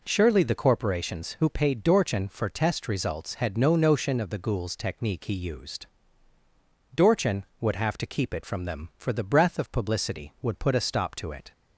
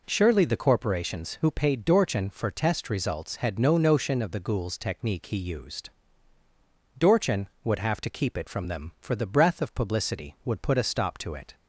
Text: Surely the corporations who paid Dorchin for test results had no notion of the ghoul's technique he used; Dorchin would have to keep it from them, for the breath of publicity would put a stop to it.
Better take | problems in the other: neither | none

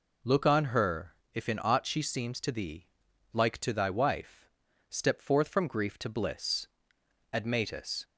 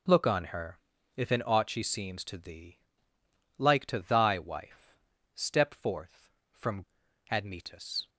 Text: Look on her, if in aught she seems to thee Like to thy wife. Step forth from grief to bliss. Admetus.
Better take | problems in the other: first | pauses between "thee" and "Like"; noticeable; at 2.7 s; 0.78 s long; also in the first // skips "grief to bliss"; at 7.0 s

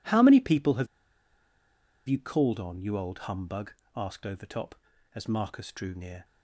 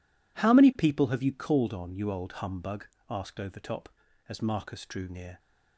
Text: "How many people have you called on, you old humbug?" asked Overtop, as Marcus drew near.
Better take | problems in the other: second | pauses between "have" and "you"; at 0.8 s; 1.2 s long

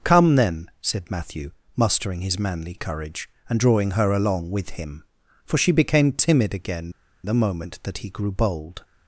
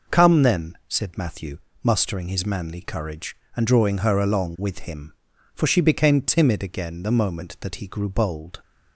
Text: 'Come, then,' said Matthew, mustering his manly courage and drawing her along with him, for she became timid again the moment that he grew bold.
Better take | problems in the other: second | pauses between "again" and "the"; slight; at 6.9 s; 0.33 s long

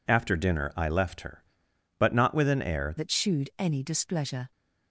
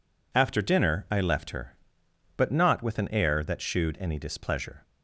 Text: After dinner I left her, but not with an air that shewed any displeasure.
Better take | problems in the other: second | changes voice at "that"; from 2.9 s on; 1.6 s long

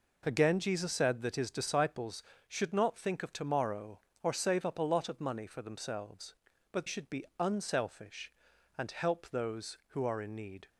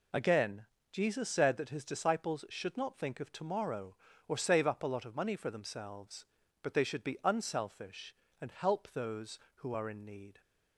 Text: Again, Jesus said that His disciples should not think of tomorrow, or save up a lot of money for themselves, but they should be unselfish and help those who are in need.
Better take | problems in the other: second | skips "they"; at 6.8 s // pauses between "be" and "unselfish"; slight; at 7.2 s; 0.16 s long

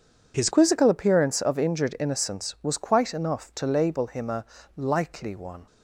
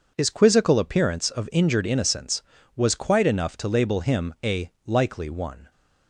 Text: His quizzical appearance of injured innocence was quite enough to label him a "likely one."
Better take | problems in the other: second | changes voice at "quizzical"; from 0.5 s on; 5.1 s long // pauses between "a" and "likely"; slight; at 4.4 s; 0.32 s long

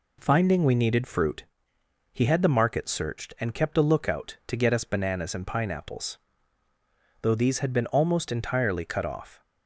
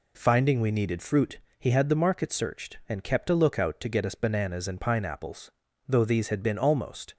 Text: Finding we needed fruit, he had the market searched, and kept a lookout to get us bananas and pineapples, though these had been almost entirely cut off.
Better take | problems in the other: first | stops before "entirely cut off"; at 7.1 s

